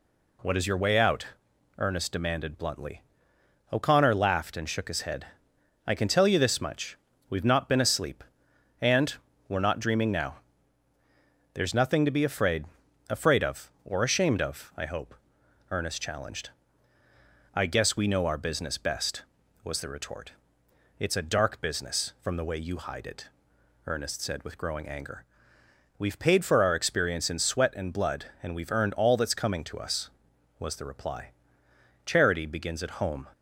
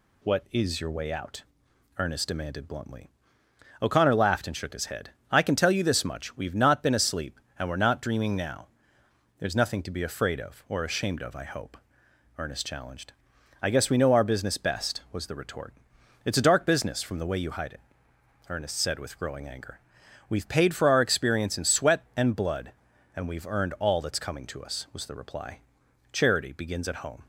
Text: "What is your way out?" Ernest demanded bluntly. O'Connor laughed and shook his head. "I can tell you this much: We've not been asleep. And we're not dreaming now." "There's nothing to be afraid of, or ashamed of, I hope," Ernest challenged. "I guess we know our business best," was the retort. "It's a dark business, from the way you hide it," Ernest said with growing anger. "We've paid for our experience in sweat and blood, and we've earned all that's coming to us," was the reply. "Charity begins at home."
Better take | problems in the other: second | pauses between "And" and "we're"; slight; at 9.1 s; 0.34 s long // says "afraid" twice; at 13.0 s

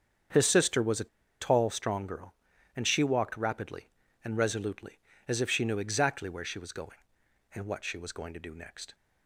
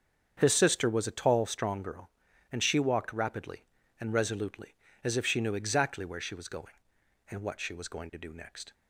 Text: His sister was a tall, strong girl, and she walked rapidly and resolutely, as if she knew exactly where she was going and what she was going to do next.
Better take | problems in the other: second | starts louder than the rest; strong; until 1.6 s; 7.5 dB; strong in the second // pauses between "a" and "tall"; slight; at 1.0 s; 0.32 s long

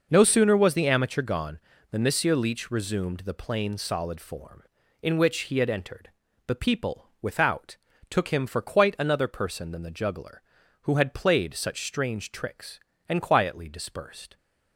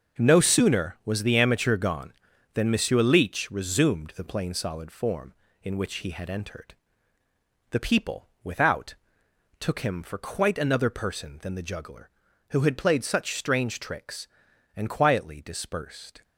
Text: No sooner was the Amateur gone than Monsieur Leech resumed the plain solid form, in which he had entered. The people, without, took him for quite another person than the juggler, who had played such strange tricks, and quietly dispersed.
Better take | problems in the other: neither | none

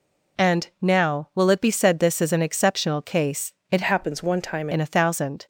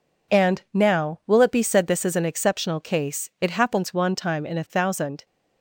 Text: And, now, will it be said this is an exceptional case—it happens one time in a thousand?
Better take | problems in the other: second | changes voice from "happens" to "time"; from 3.8 to 4.6 s; 0.8 s long

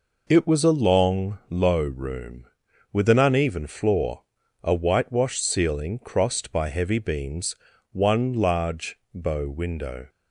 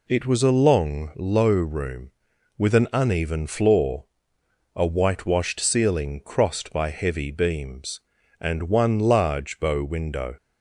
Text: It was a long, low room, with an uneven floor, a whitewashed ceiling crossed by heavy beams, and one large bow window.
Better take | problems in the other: second | skips "and"; at 7.7 s // pauses between "large" and "bow"; slight; at 8.9 s; 0.18 s long

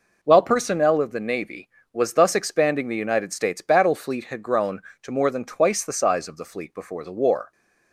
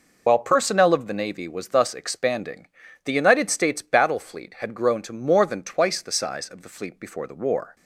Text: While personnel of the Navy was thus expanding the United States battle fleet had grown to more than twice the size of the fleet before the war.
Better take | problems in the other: first | loses the start of "While"; at 0.2 s; 55 ms // pauses between "expanding" and "the"; at 2.6 s; 0.38 s long

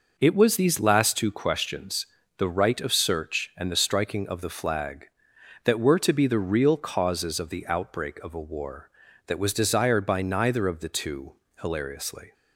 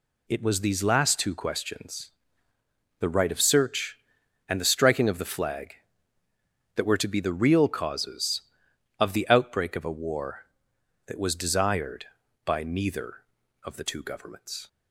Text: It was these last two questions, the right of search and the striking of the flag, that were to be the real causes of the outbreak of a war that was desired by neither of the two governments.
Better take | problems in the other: second | says "hilariously" for "governments"; at 11.6 s

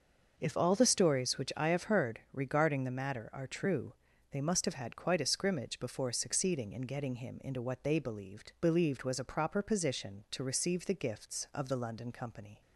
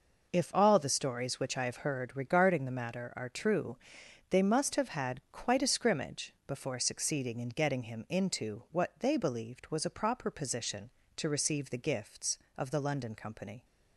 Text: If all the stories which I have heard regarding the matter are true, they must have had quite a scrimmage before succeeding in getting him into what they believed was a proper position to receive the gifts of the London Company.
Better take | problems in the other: second | starts louder than the rest; until 1.3 s; 6 dB // says "believed" twice; at 8.6 s

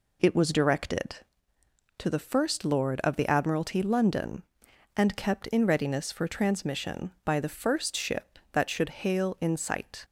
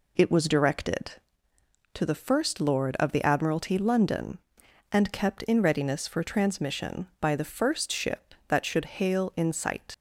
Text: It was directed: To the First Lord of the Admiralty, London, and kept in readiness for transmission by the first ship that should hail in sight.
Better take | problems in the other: first | leaves "sight" unfinished; at 9.9 s; 60 ms

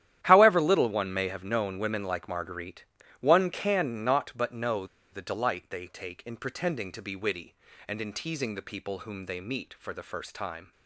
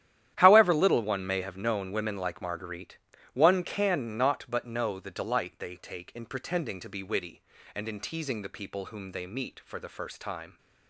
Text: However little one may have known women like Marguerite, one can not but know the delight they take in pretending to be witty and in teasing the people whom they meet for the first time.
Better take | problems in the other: second | starts louder than the rest; strong; until 1.2 s; 11.5 dB; strong in the second // pauses between "know" and "the"; slight; at 4.8 s; 0.26 s long

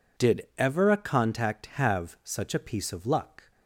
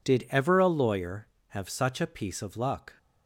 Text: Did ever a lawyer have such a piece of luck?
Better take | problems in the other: second | says "contact" for "lawyer"; at 0.9 s

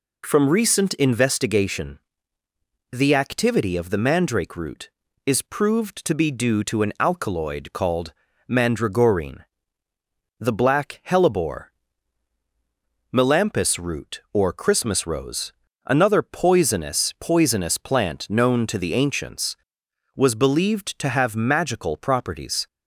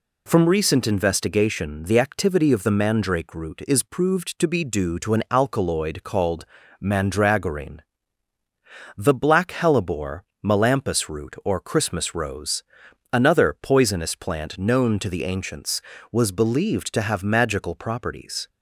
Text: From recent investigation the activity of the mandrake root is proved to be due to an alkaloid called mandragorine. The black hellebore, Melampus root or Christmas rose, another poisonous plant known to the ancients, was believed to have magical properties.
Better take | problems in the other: second | pauses between "investigation" and "the"; noticeable; at 1.9 s; 0.92 s long // pauses between "called" and "mandragorine"; slight; at 8.1 s; 0.36 s long; also in the second // says "poisonous" twice; at 17.1 s

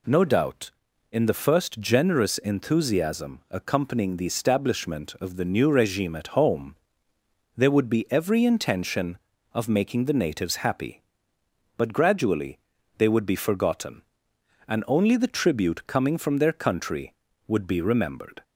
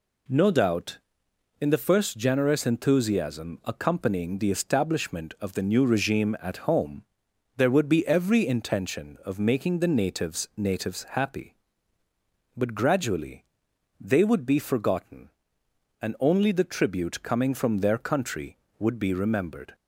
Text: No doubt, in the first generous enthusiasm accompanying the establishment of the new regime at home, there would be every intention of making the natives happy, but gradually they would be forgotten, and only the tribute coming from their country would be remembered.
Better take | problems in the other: first | says "natives" twice; at 10.5 s // pauses between "gradually" and "they"; noticeable; at 13.4 s; 0.56 s long; also in the first

